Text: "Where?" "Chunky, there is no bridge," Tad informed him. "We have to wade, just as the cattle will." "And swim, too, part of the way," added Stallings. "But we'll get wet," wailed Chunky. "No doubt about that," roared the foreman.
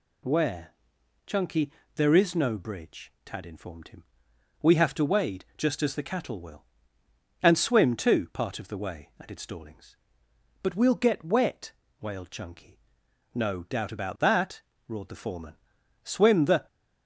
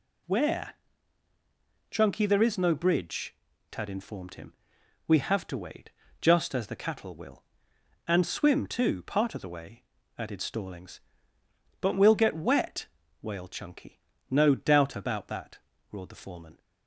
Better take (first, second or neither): second